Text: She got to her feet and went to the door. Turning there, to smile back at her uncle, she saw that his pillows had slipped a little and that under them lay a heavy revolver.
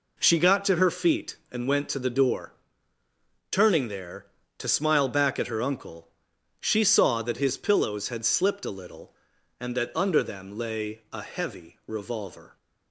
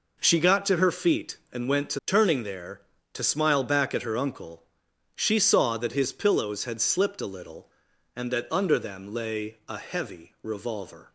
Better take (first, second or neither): first